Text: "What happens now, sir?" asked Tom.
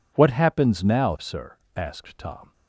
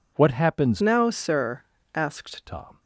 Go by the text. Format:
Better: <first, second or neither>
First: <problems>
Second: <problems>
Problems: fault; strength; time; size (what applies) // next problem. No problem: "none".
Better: first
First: none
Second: changes voice from "now" to "asked"; from 0.7 to 2.4 s; 1.7 s long